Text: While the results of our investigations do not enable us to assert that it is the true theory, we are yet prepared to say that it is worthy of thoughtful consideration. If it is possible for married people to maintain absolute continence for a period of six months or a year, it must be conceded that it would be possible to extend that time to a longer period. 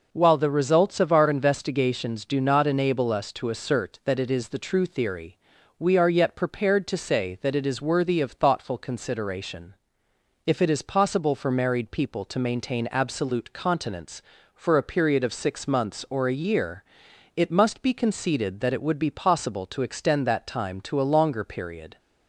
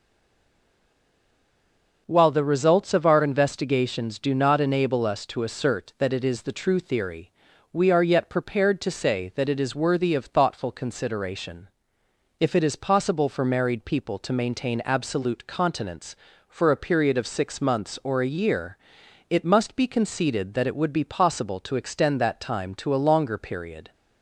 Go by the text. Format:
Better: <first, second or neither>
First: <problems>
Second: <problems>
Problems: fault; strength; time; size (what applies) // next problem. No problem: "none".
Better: first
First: none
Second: stays silent before the first word; noticeable; until 2.0 s; 2.0 s long